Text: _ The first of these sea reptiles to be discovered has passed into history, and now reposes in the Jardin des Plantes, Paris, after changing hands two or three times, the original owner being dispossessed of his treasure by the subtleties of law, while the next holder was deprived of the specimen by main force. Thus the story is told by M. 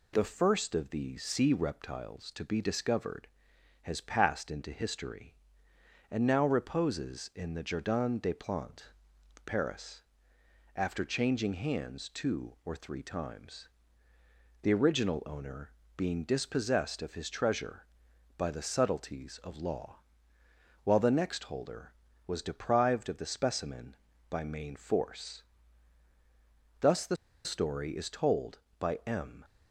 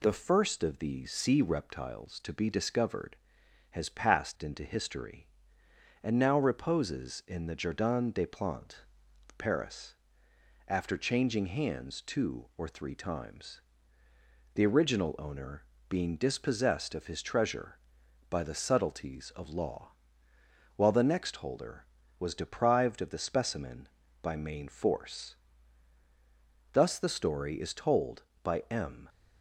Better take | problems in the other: second | pauses between "owner" and "being"; slight; at 15.7 s; 0.24 s long; slight in the second // pauses between "the" and "story"; slight; at 27.1 s; 0.28 s long

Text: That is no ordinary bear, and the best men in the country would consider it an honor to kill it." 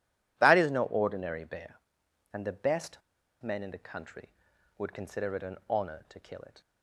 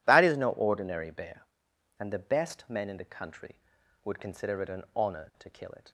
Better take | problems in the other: second | pauses between "best" and "men"; at 3.0 s; 0.41 s long

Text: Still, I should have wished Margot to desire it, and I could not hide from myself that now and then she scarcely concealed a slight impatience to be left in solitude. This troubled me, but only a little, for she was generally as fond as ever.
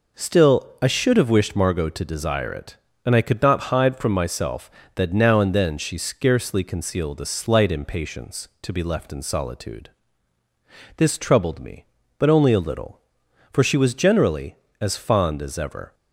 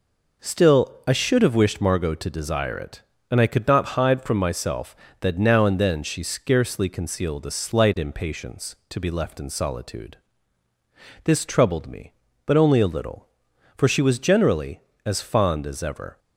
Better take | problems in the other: neither | none

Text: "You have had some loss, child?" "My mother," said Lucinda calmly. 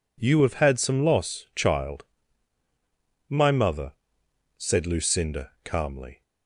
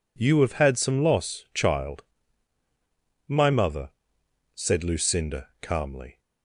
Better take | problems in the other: neither | none

